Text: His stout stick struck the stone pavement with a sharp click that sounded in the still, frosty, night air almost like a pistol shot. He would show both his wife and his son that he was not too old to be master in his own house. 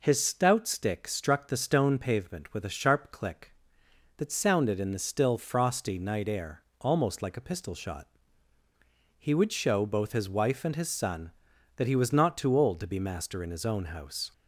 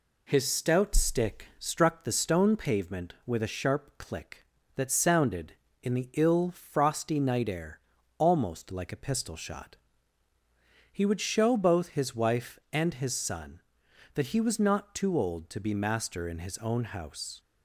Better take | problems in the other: first | says "ill" for "still"; at 6.1 s // pauses between "air" and "almost"; at 7.7 s; 0.38 s long; slight in the first

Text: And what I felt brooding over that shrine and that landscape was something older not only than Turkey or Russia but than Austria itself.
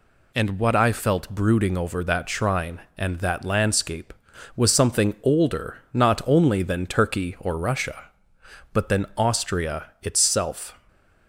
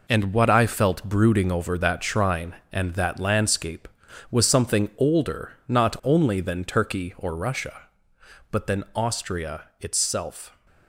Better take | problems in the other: first | gets quieter; throughout; 7 dB // pauses between "Austria" and "itself"; slight; at 9.6 s; 0.16 s long; slight in the first

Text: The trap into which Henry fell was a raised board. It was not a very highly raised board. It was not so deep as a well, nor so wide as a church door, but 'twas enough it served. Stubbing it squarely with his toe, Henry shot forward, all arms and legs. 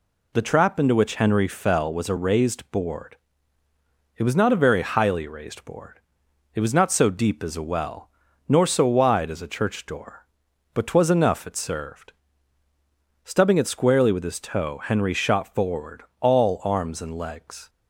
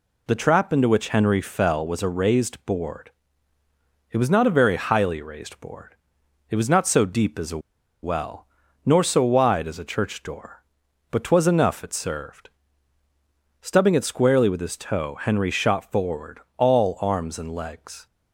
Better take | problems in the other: first | pauses between "a" and "well"; at 7.5 s; 0.44 s long

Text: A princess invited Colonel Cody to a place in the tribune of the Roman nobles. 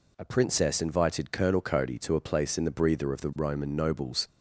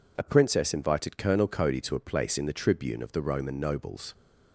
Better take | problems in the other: second | says "breather" for "tribune"; at 2.7 s

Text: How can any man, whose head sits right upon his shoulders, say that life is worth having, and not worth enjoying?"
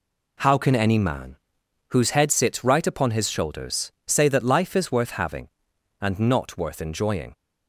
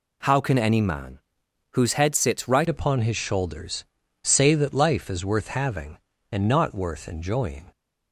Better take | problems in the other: first | changes voice at "upon"; from 2.6 s on; 5.1 s long

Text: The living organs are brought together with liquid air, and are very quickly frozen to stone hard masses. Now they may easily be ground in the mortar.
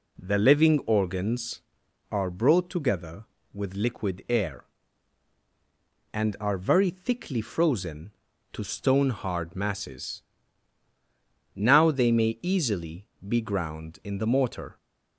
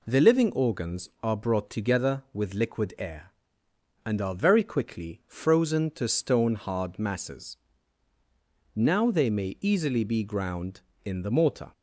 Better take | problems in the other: second | says "thickly" for "quickly"; at 6.8 s // pauses between "easily" and "be"; slight; at 13.0 s; 0.20 s long

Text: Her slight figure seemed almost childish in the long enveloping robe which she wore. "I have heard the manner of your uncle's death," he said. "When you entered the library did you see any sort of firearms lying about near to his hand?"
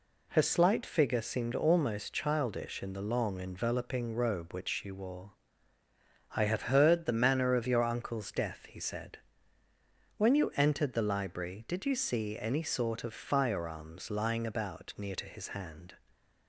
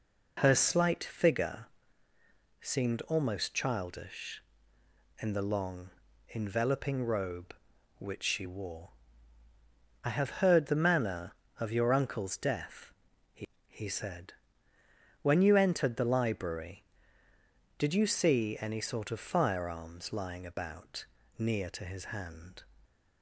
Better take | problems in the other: first | pauses between "figure" and "seemed"; noticeable; at 1.6 s; 0.94 s long // pauses between "long" and "enveloping"; at 5.9 s; 0.38 s long // says "he" twice; at 13.6 s // pauses between "about" and "near"; slight; at 21.0 s; 0.32 s long

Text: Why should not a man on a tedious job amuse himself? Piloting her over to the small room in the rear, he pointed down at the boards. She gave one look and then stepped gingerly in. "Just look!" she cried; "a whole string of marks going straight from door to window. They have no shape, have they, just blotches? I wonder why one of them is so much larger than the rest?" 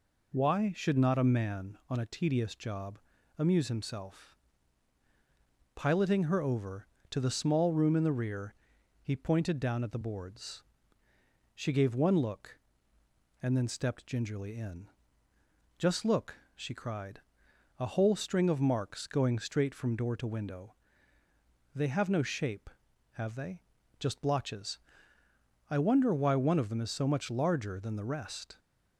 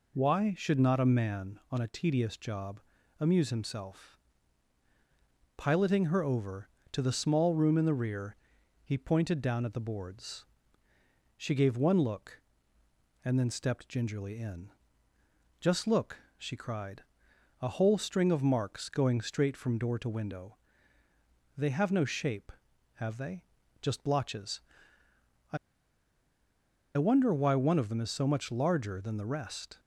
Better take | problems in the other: first | pauses between "job" and "amuse"; at 2.7 s; 0.40 s long; also in the first // pauses between "I" and "wonder"; strong; at 25.5 s; 1.4 s long

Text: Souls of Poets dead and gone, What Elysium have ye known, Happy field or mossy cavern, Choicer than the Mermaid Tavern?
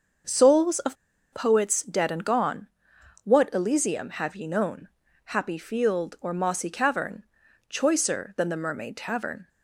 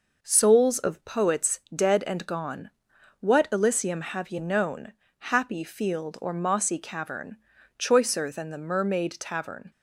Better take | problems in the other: second | starts louder than the rest; until 1.6 s; 6.5 dB // pauses between "of" and "Poets"; at 0.9 s; 0.38 s long

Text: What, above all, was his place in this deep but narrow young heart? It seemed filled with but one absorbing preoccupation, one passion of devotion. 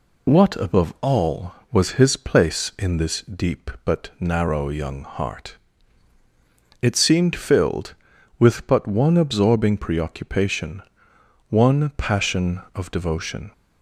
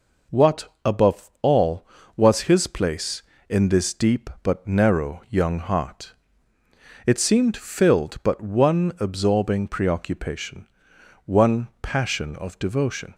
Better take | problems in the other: first | skips "with"; at 8.2 s

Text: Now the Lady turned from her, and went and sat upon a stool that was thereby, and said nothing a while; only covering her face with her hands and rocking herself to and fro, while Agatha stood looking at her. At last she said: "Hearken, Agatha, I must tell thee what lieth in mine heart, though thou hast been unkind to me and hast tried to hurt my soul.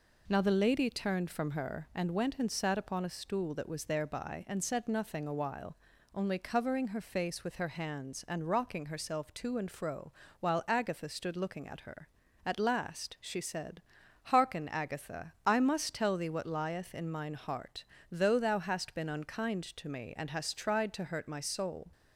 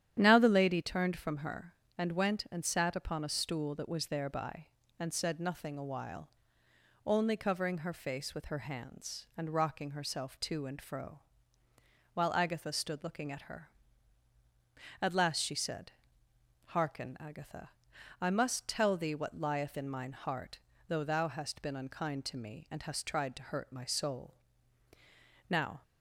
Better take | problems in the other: first | starts louder than the rest; strong; until 1.2 s; 10.5 dB // goes on to say "Now"; slight; from 25.4 s on; 0.34 s long

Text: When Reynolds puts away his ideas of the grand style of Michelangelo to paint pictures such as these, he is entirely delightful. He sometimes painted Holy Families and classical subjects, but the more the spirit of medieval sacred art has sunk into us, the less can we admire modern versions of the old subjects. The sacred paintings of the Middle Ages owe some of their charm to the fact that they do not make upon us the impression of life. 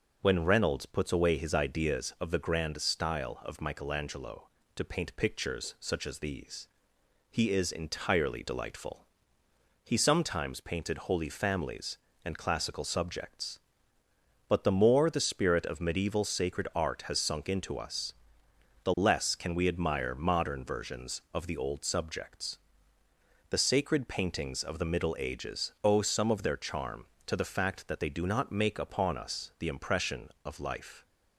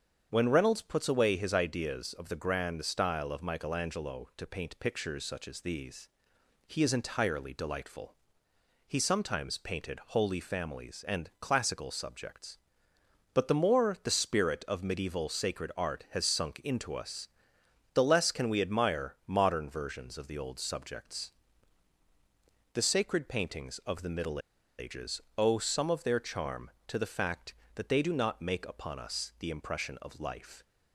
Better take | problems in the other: first | starts louder than the rest; strong; until 1.3 s; 7.5 dB // pauses between "Middle" and "Ages"; at 24.3 s; 0.39 s long // pauses between "Ages" and "owe"; slight; at 25.2 s; 0.16 s long

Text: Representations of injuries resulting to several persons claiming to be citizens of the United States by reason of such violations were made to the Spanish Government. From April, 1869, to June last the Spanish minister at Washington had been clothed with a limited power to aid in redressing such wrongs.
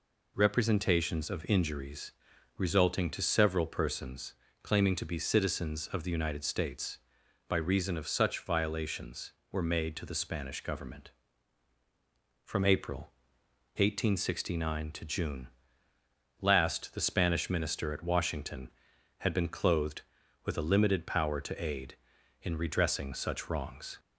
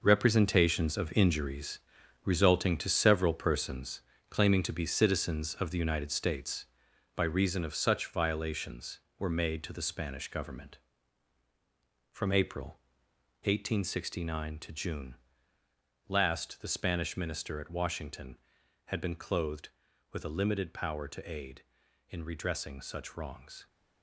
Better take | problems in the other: first | gets quieter; strong; throughout; 10.5 dB // pauses between "injuries" and "resulting"; noticeable; at 1.7 s; 0.46 s long; noticeable in the first // pauses between "persons" and "claiming"; slight; at 4.0 s; 0.30 s long; slight in the first // pauses between "June" and "last"; noticeable; at 15.1 s; 0.94 s long; noticeable in the first

